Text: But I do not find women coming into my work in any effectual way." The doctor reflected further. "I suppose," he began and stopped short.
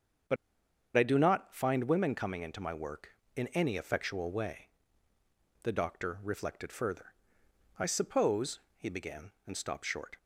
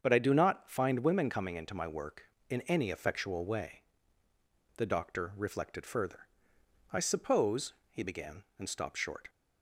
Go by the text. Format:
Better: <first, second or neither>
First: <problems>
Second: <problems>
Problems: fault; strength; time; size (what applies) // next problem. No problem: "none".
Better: second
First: starts louder than the rest; until 1.9 s; 6.5 dB // pauses between "But" and "I"; noticeable; at 0.3 s; 0.61 s long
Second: starts louder than the rest; until 1.0 s; 7 dB